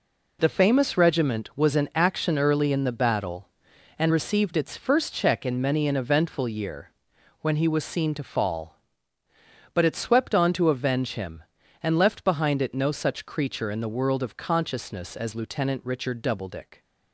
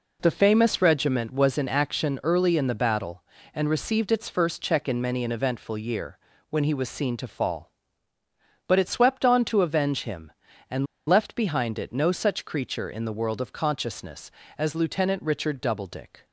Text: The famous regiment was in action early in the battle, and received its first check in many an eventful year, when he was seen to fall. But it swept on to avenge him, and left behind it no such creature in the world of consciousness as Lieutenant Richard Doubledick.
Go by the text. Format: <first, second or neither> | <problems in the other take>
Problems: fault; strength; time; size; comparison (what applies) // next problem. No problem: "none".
first | pauses between "and" and "left"; slight; at 10.8 s; 0.21 s long